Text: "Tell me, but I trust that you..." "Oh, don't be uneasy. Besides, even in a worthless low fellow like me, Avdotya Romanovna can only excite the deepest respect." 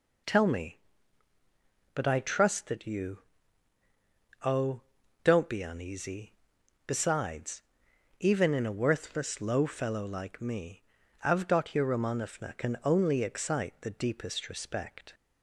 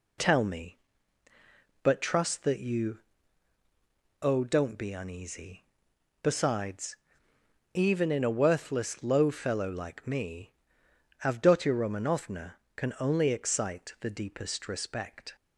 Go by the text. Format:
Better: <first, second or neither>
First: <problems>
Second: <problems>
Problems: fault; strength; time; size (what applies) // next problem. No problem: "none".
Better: first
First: none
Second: skips "I"; at 2.0 s